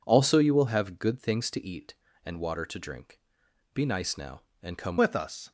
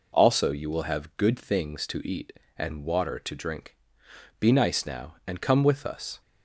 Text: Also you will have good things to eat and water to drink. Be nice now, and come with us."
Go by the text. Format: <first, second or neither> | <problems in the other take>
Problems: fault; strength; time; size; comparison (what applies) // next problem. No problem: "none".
second | changes voice at "with"; from 4.9 s on; 0.6 s long